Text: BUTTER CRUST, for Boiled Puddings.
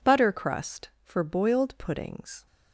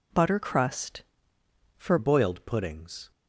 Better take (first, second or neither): first